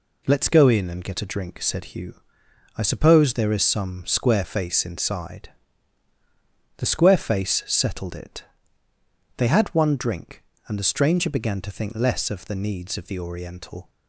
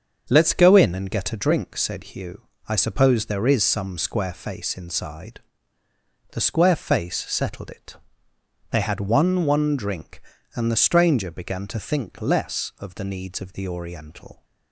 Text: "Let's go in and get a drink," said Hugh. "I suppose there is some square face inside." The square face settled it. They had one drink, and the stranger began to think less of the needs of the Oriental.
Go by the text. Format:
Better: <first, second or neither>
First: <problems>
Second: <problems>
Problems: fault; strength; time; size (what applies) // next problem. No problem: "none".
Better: first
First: none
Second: starts louder than the rest; until 1.3 s; 7 dB // says "one" twice; at 9.4 s